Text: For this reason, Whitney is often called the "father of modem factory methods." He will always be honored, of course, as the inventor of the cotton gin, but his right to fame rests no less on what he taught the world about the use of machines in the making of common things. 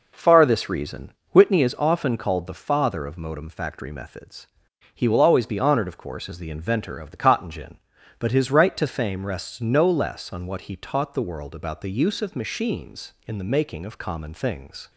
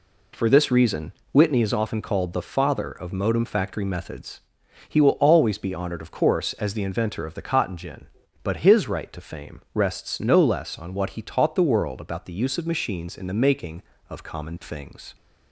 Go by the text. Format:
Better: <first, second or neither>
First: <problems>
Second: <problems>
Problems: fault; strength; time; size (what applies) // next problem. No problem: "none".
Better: second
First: says "Far" for "For"; at 0.1 s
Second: none